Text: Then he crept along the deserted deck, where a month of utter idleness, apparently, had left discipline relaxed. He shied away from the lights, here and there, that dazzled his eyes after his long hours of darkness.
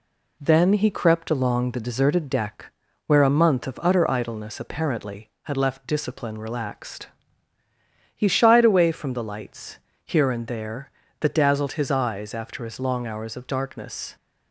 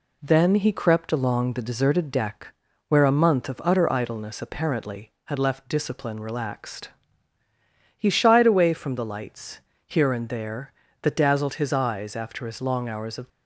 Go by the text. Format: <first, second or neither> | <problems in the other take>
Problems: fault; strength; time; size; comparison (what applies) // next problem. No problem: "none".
first | stops before "darkness"; at 13.2 s